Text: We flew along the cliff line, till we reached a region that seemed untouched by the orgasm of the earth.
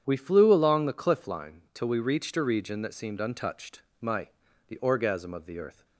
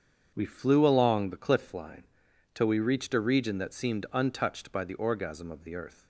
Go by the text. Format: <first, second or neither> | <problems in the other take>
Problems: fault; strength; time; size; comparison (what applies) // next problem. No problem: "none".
second | starts louder than the rest; strong; until 1.0 s; 8 dB; strong in the second // says "my" for "by"; at 4.0 s